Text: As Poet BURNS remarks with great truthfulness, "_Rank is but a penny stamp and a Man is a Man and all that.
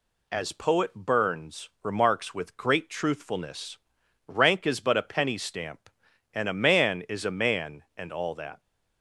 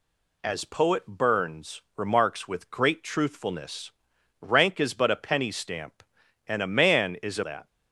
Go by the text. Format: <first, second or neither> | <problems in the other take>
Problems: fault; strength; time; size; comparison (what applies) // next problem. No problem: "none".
first | pauses between "BURNS" and "remarks"; slight; at 1.8 s; 0.16 s long // skips "Man and all"; at 7.4 s